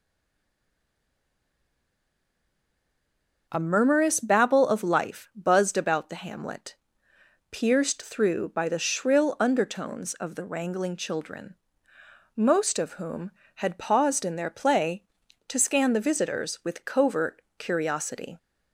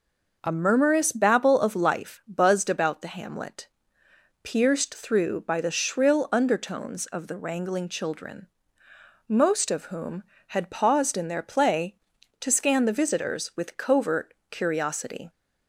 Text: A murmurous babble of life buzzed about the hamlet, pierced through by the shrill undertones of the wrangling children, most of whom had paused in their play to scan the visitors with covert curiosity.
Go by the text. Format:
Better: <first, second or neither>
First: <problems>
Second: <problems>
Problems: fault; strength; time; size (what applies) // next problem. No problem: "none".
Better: second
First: stays silent before the first word; strong; until 3.4 s; 3.4 s long // pauses between "covert" and "curiosity"; slight; at 17.4 s; 0.16 s long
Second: pauses between "covert" and "curiosity"; slight; at 14.3 s; 0.16 s long